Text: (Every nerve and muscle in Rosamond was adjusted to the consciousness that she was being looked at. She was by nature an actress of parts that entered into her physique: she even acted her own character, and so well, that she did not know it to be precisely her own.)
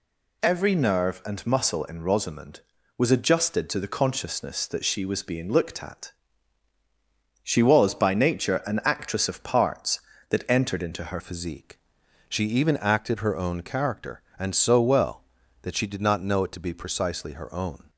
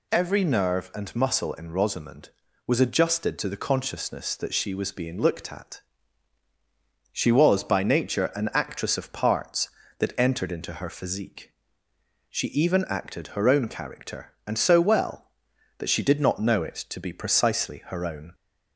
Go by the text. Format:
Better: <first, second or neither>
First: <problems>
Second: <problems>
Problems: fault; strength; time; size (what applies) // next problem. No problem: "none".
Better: second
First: changes voice at "physique"; from 11.1 s on; 6.7 s long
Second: none